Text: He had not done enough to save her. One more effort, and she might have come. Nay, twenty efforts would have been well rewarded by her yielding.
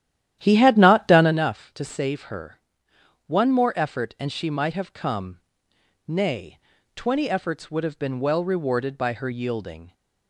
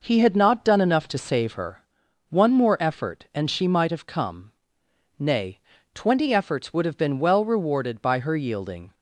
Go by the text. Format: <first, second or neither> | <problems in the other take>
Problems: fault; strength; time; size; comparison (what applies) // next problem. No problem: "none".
second | starts louder than the rest; strong; until 1.5 s; 11.5 dB